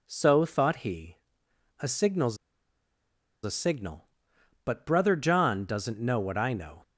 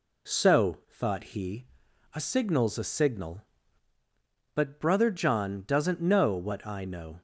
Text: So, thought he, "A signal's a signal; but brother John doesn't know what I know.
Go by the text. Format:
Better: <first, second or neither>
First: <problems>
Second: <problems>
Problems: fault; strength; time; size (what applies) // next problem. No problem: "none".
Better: second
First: pauses between "signal's" and "a"; at 2.3 s; 1.0 s long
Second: none